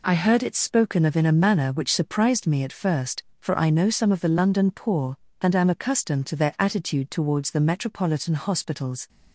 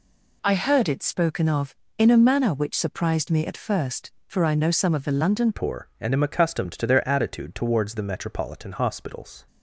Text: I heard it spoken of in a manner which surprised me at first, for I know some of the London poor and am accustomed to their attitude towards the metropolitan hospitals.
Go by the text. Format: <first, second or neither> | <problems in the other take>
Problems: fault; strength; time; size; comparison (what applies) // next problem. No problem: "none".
first | changes voice at "poor"; from 5.5 s on; 3.9 s long